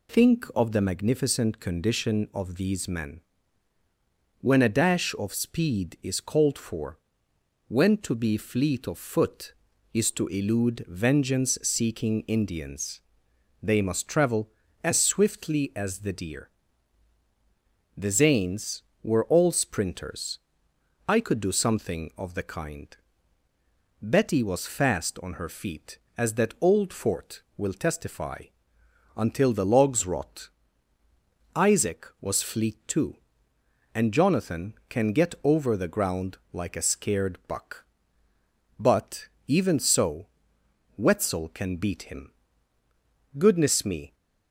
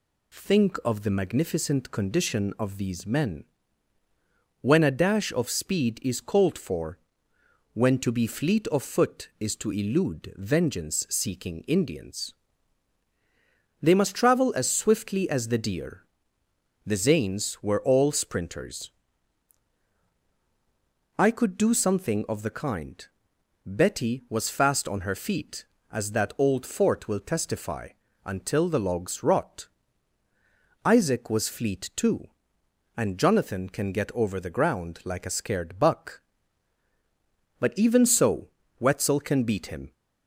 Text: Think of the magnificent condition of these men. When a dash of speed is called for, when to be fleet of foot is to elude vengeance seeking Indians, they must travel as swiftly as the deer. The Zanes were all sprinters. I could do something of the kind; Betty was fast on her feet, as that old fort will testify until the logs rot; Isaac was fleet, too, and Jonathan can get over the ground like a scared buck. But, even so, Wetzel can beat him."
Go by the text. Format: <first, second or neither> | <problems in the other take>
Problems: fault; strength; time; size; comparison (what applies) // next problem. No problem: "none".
second | pauses between "testify" and "until"; noticeable; at 28.4 s; 0.70 s long; slight in the second // goes on to say "Goodness me"; noticeable; from 43.3 s on; 0.78 s long